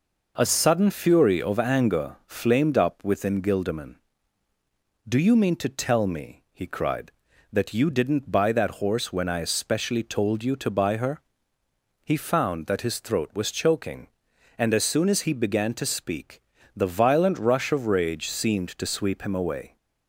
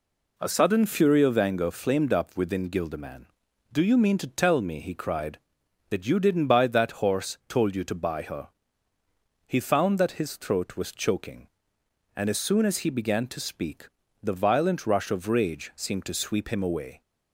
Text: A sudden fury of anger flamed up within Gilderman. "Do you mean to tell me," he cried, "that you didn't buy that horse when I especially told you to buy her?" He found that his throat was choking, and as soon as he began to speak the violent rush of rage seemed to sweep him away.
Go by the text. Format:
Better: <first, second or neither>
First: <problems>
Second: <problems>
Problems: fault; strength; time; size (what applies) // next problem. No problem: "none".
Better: first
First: pauses between "speak" and "the"; slight; at 16.4 s; 0.34 s long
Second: skips "when I especially"; at 7.4 s // pauses between "speak" and "the"; slight; at 13.8 s; 0.34 s long